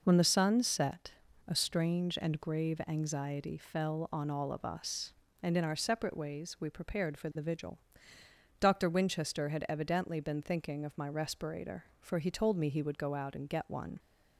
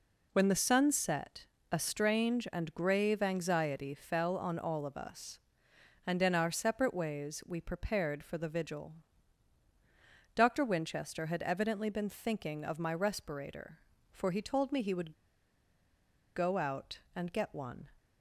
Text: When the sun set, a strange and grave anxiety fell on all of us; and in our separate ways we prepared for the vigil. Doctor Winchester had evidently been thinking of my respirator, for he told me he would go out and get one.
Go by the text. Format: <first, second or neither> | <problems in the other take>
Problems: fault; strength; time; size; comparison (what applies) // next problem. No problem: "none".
first | pauses between "would" and "go"; at 15.1 s; 1.2 s long